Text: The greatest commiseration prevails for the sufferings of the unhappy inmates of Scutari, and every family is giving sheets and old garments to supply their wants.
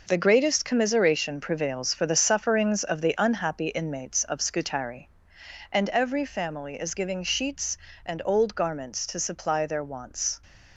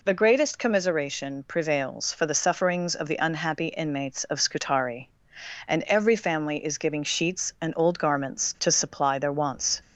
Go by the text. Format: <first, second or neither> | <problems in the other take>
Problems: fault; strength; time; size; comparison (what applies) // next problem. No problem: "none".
second | gets quieter; strong; throughout; 8.5 dB